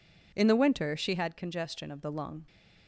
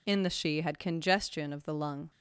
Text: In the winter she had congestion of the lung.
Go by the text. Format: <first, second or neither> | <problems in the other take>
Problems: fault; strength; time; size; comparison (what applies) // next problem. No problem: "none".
first | skips "winter"; at 0.3 s